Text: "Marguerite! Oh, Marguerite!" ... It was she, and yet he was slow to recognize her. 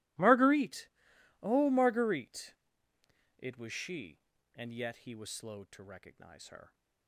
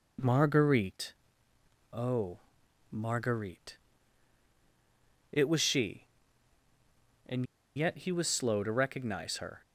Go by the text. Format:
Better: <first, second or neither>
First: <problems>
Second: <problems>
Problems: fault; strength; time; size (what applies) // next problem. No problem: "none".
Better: first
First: none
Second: pauses between "and" and "yet"; slight; at 7.4 s; 0.30 s long